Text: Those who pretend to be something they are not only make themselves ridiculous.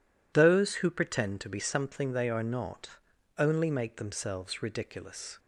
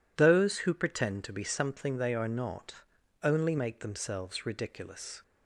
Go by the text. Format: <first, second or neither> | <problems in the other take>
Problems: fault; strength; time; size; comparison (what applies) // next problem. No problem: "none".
neither | pauses between "not" and "only"; noticeable; the same in both